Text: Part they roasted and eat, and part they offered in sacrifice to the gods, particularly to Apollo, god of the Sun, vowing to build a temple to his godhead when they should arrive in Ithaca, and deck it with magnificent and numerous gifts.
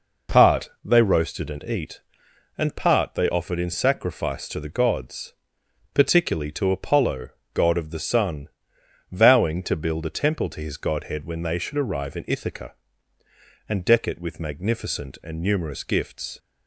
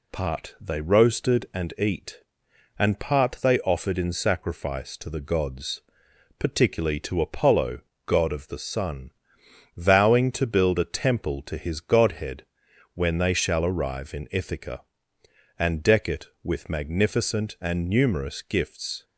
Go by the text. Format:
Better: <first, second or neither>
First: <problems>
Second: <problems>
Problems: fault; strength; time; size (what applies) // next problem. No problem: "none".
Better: first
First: none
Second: pauses between "godhead" and "when"; noticeable; at 12.4 s; 0.50 s long // says "shall" for "should"; at 13.3 s